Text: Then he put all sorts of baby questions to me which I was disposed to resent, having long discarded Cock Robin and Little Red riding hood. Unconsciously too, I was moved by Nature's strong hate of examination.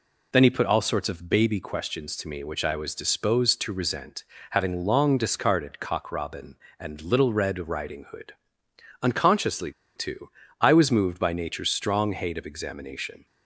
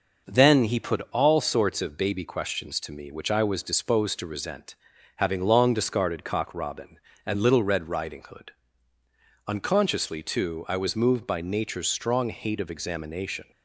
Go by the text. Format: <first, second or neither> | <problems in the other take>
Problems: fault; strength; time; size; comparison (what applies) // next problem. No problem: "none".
second | pauses between "Unconsciously" and "too"; slight; at 9.7 s; 0.24 s long